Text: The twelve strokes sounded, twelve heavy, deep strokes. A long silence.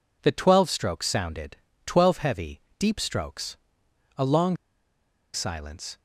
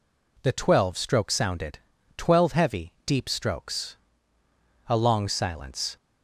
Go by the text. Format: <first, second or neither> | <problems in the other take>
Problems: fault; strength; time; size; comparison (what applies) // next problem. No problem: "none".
second | pauses between "long" and "silence"; noticeable; at 4.5 s; 0.78 s long